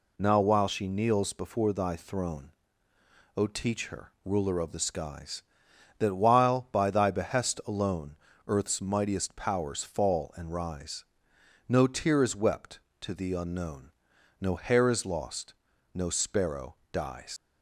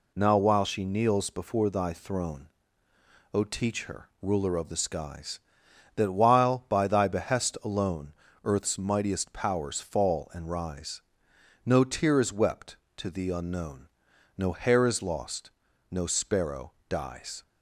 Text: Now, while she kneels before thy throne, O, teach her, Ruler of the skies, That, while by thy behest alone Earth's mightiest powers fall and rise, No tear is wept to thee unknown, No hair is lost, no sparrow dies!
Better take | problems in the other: second | pauses between "alone" and "Earth's"; slight; at 8.1 s; 0.30 s long; slight in the second // pauses between "sparrow" and "dies"; slight; at 16.7 s; 0.16 s long; slight in the second // leaves "dies" unfinished; at 17.3 s; 90 ms

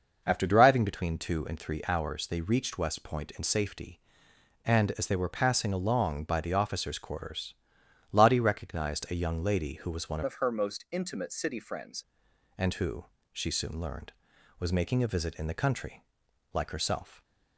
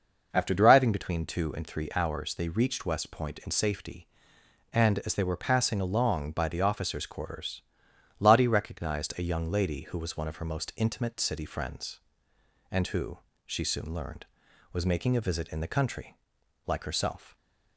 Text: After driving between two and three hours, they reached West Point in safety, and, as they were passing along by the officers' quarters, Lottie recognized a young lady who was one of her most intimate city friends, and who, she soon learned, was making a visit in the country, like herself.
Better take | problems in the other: second | changes voice from "of" to "friends"; from 10.2 to 12.0 s; 1.8 s long

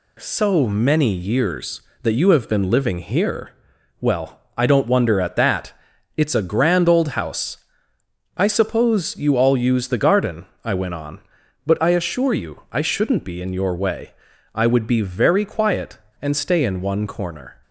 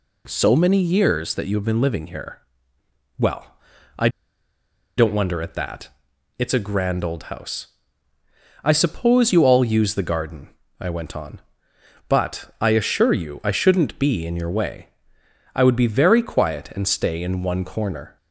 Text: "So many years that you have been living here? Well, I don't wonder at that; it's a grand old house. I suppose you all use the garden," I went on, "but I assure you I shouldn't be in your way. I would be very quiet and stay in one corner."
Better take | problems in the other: first | pauses between "I" and "don't"; noticeable; at 4.0 s; 0.89 s long

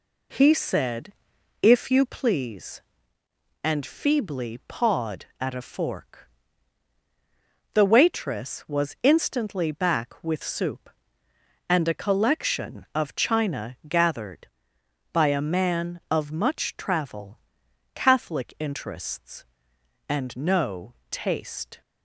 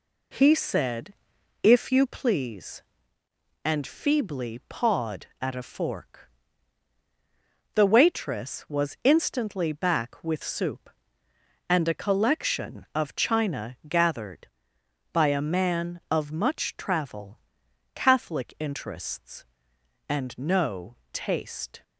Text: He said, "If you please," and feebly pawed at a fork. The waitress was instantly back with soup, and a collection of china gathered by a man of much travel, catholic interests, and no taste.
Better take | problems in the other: neither | pauses between "no" and "taste"; slight; the same in both

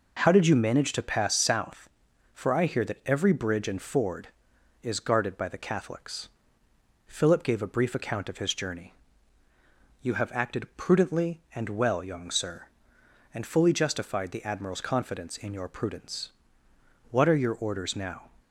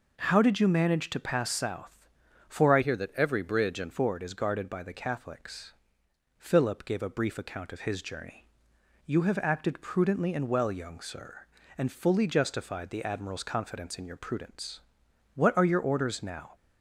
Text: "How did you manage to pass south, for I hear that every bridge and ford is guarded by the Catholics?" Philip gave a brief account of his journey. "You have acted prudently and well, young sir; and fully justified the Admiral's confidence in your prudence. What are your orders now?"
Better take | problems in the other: first | changes voice from "hear" to "and"; from 2.8 to 3.9 s; 1.1 s long

